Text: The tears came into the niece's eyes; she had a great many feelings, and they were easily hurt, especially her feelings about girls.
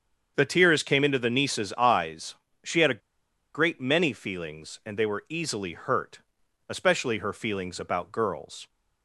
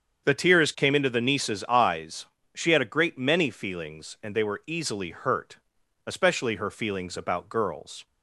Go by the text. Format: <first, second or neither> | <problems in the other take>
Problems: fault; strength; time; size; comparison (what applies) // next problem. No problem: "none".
second | starts louder than the rest; strong; until 1.3 s; 7 dB; strong in the second // pauses between "a" and "great"; noticeable; at 2.9 s; 0.54 s long